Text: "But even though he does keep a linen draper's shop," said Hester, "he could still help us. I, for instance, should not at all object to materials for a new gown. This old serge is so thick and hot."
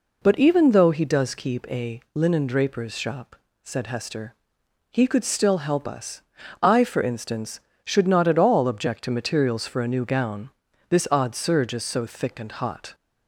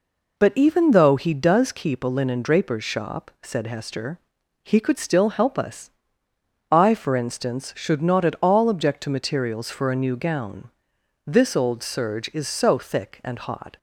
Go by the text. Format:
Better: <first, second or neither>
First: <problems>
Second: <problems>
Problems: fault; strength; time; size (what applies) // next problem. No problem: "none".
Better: second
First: says "odd" for "old"; at 11.1 s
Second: none